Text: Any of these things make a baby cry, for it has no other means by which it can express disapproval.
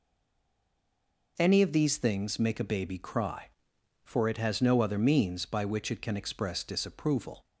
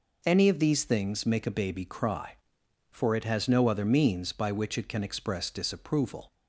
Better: second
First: stays silent before the first word; noticeable; until 1.3 s; 1.3 s long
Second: none

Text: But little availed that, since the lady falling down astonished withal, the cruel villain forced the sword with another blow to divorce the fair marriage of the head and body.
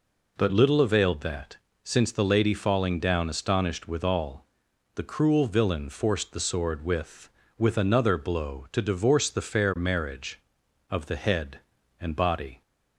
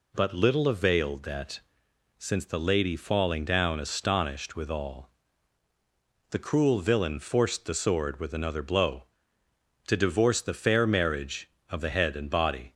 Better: second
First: says "with" twice; at 7.5 s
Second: none

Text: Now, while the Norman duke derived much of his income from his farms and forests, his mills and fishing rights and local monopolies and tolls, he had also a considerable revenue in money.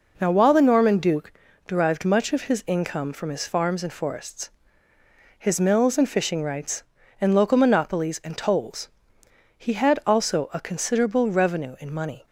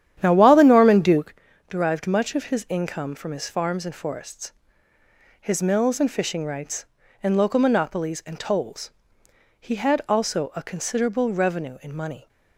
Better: first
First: pauses between "duke" and "derived"; slight; at 1.3 s; 0.34 s long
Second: starts louder than the rest; strong; until 1.4 s; 10 dB // pauses between "duke" and "derived"; slight; at 1.3 s; 0.34 s long

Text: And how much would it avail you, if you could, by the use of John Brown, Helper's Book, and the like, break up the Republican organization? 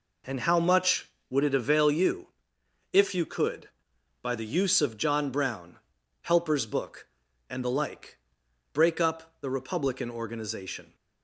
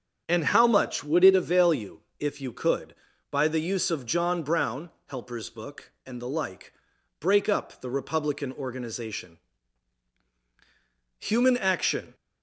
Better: first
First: none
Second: starts louder than the rest; strong; until 1.2 s; 7.5 dB // goes on to say "Human action"; noticeable; from 11.1 s on; 0.96 s long

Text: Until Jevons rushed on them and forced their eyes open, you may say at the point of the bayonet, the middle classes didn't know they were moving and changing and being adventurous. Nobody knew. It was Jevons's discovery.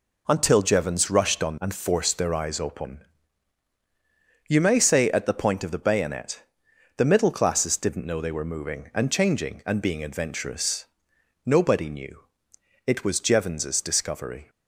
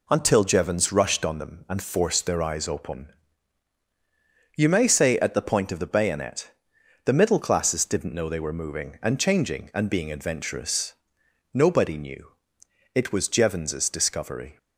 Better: second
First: skips "them"; at 1.5 s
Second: none

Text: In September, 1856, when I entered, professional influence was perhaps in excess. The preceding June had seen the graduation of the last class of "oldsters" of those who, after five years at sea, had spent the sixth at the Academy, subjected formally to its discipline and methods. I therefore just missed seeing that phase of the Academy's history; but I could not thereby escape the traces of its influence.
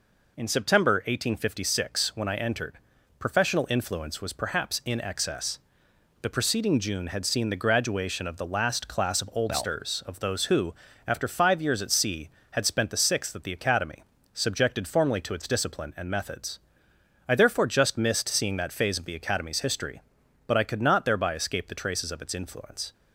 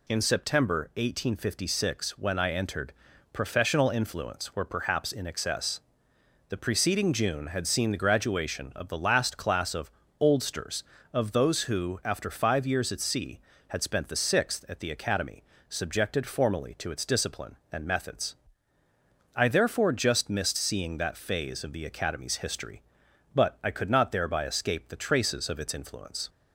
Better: first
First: none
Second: says "were" for "was"; at 4.5 s // pauses between "of" and "oldsters"; slight; at 9.9 s; 0.30 s long

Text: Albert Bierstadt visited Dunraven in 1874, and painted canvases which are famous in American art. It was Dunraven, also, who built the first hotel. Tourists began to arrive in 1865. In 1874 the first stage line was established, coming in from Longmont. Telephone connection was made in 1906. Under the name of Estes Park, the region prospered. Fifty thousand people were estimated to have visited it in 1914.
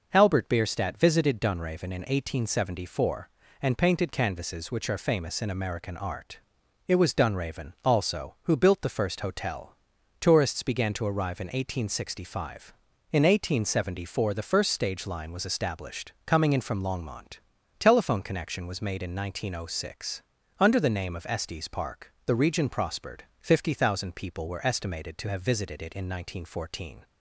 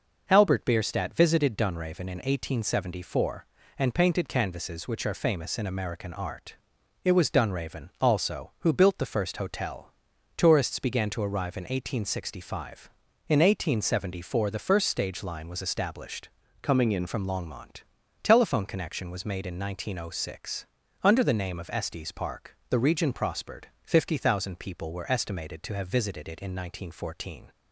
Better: first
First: none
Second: changes voice from "coming" to "in"; from 16.6 to 17.0 s; 0.4 s long

